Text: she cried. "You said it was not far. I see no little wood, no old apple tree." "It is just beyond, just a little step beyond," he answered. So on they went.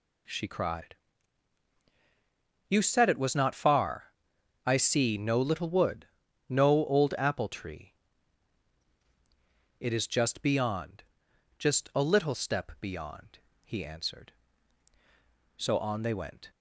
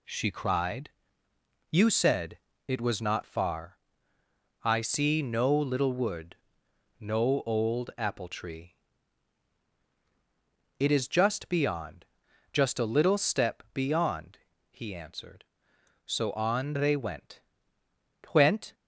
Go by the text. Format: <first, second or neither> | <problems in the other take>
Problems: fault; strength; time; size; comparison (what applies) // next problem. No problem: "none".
first | pauses between "said" and "it"; slight; at 2.3 s; 0.30 s long // says "went" twice; at 18.3 s